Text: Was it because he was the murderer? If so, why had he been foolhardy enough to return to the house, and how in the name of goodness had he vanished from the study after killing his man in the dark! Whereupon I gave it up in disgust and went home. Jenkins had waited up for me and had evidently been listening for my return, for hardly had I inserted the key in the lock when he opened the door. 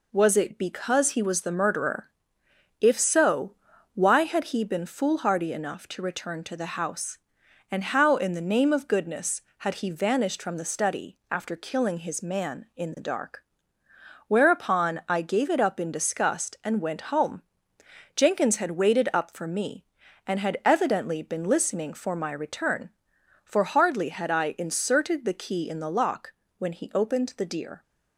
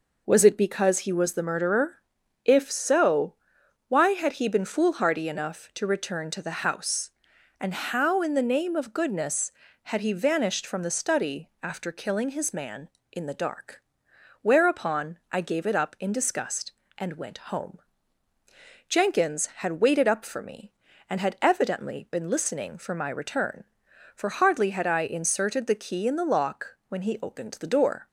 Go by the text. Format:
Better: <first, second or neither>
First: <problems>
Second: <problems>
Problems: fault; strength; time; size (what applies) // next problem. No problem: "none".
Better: second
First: pauses between "lock" and "when"; slight; at 26.3 s; 0.24 s long // says "deer" for "door"; at 27.4 s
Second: none